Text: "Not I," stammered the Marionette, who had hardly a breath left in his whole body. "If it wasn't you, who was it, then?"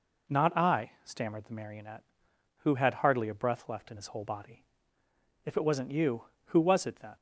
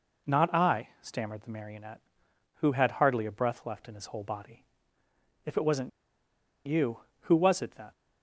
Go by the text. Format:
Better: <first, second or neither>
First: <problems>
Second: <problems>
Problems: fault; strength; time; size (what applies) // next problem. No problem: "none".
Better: first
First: none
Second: pauses between "wasn't" and "you"; noticeable; at 5.8 s; 0.75 s long